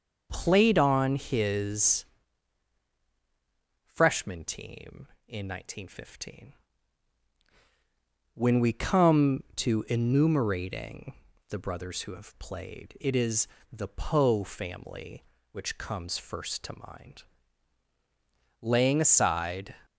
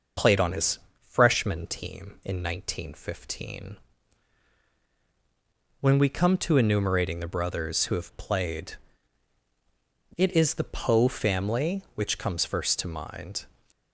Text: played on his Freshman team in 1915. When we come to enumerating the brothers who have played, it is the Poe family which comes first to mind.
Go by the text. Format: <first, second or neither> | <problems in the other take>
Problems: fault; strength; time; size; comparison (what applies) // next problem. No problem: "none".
second | starts louder than the rest; until 1.3 s; 6 dB // pauses between "his" and "Freshman"; strong; at 2.0 s; 1.8 s long; slight in the second // pauses between "enumerating" and "the"; slight; at 11.1 s; 0.36 s long // pauses between "is" and "the"; slight; at 13.4 s; 0.24 s long // goes on to say "Laying aside"; noticeable; from 18.6 s on; 1.1 s long